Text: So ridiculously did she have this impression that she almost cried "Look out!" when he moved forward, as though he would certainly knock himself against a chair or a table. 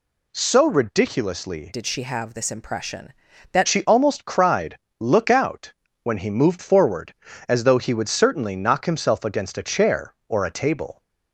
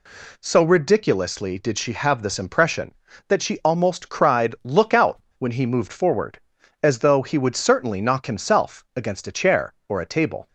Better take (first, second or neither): second